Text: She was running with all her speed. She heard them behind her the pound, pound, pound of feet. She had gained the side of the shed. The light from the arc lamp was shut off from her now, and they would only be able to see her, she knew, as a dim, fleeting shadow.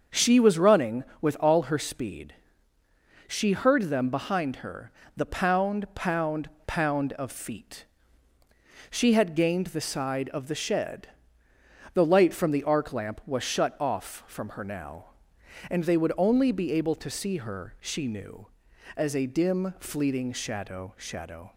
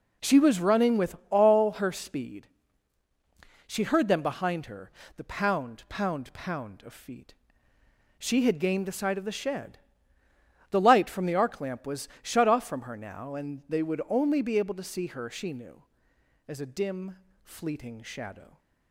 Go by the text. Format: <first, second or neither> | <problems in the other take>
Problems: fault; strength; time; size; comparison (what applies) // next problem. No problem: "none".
second | starts louder than the rest; until 1.2 s; 6.5 dB // pauses between "her" and "the"; slight; at 4.9 s; 0.26 s long; slight in the second // says "shadow" twice; at 20.9 s